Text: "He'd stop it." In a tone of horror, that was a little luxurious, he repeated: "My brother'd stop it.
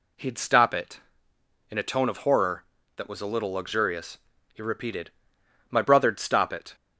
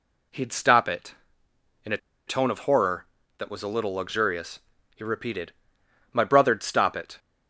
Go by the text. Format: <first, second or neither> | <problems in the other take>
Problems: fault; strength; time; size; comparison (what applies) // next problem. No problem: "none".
first | pauses between "a" and "tone"; slight; at 1.9 s; 0.30 s long